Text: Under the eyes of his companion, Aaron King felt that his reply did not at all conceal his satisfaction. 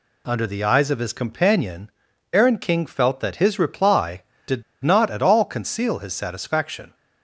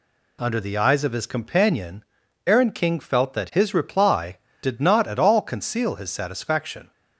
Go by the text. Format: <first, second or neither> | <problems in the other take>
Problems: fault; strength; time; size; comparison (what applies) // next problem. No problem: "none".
second | pauses between "did" and "not"; slight; at 4.6 s; 0.21 s long